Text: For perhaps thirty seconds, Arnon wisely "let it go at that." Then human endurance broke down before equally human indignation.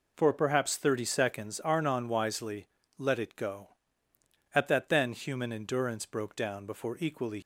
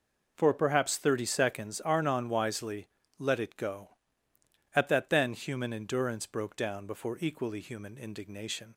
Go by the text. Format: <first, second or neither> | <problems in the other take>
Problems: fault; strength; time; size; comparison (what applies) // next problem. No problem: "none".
second | pauses between "wisely" and "let"; slight; at 2.6 s; 0.32 s long; slight in the second // stops before "human indignation"; at 7.4 s